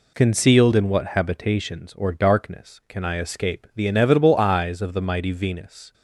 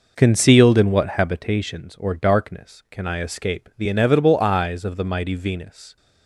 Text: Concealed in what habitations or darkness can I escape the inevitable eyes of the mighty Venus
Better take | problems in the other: first | starts louder than the rest; noticeable; until 1.4 s; 5 dB

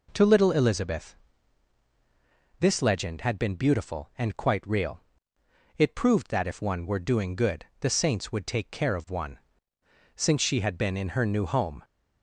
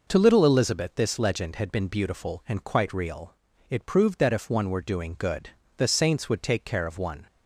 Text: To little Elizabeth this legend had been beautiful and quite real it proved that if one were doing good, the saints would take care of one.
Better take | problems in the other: second | pauses between "Elizabeth" and "this"; strong; at 1.1 s; 1.4 s long // pauses between "real" and "it"; noticeable; at 4.9 s; 0.78 s long; slight in the second // goes on to say "Since she had been in her new home"; strong; from 10.1 s on; 1.6 s long

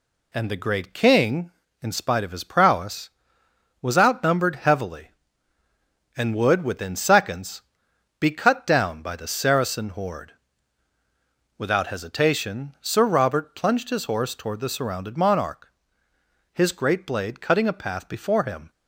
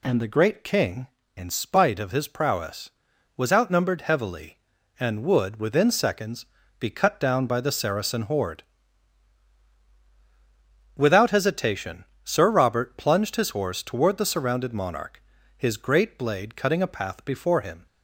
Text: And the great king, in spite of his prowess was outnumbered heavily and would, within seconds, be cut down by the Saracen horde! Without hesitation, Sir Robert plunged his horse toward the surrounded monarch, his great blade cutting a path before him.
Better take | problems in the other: neither | none

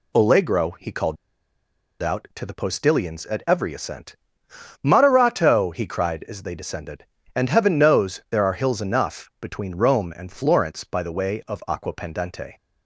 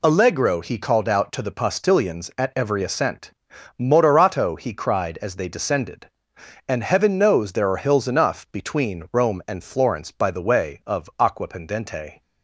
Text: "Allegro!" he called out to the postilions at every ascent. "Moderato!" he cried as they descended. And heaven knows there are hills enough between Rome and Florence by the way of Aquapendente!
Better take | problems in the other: second | pauses between "called" and "out"; noticeable; at 1.1 s; 0.86 s long

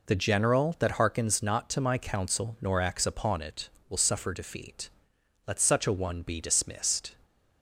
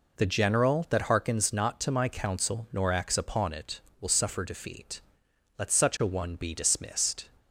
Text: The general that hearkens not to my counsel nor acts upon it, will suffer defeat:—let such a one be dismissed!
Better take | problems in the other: neither | none

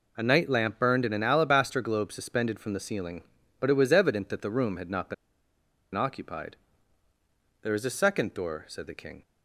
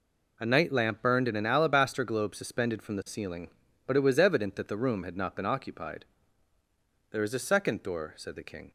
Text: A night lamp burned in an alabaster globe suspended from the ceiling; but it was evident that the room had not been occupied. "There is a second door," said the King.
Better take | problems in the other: second | pauses between "been" and "occupied"; noticeable; at 5.1 s; 0.80 s long

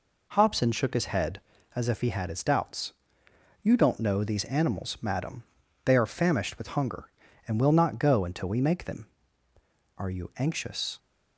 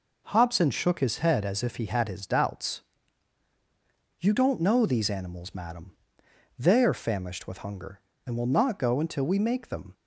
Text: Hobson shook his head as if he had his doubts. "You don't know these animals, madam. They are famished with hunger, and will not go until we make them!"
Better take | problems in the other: second | goes on to say "Are you anxious"; noticeable; from 9.9 s on; 1.0 s long

